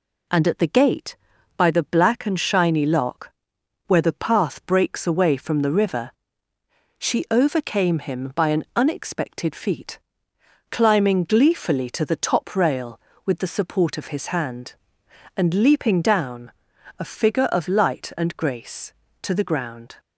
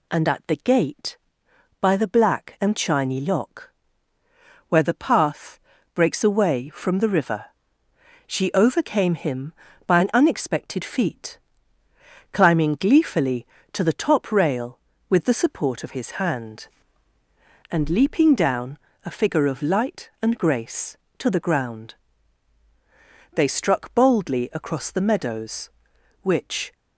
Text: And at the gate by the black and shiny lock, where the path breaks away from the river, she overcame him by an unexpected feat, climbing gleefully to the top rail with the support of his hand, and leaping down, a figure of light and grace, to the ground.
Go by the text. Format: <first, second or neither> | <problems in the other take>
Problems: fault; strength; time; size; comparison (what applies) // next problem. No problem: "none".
first | pauses between "path" and "breaks"; slight; at 5.6 s; 0.34 s long // goes on to say "They struck boldly across the meadows which"; strong; from 23.3 s on; 3.3 s long